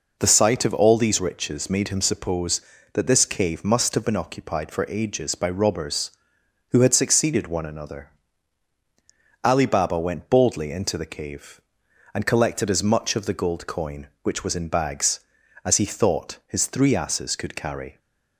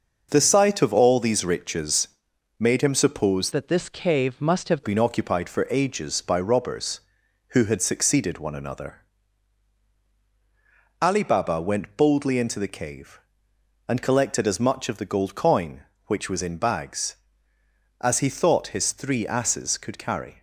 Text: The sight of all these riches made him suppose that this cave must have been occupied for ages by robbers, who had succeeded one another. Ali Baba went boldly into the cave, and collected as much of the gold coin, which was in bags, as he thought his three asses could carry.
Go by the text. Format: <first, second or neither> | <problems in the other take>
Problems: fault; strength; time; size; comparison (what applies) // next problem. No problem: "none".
first | starts louder than the rest; noticeable; until 1.3 s; 6 dB // pauses between "riches" and "made"; noticeable; at 2.0 s; 0.54 s long // changes voice from "that" to "have"; from 3.5 to 4.8 s; 1.3 s long